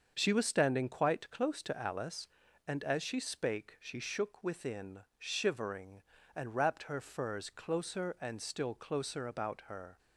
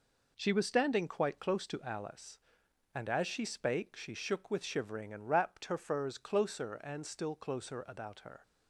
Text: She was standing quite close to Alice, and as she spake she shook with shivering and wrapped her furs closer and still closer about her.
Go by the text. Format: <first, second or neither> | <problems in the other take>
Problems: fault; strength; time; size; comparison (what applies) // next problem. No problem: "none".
second | starts louder than the rest; until 1.1 s; 6.5 dB // says "within" for "with"; at 4.4 s